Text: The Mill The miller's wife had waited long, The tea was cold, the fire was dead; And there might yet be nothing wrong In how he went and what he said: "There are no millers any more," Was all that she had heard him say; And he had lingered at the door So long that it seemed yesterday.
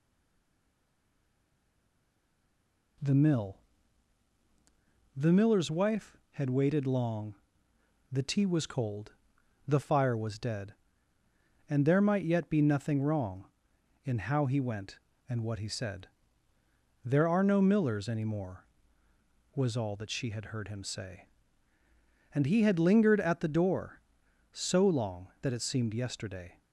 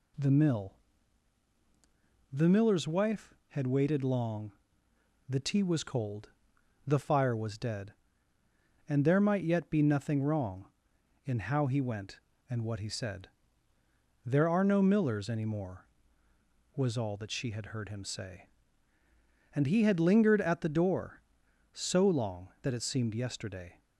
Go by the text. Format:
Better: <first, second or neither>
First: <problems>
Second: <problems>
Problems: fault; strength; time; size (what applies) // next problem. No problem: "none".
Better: second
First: stays silent before the first word; strong; until 2.9 s; 2.9 s long // pauses between "Mill" and "The"; strong; at 3.5 s; 1.5 s long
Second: pauses between "Mill" and "The"; strong; at 0.7 s; 1.5 s long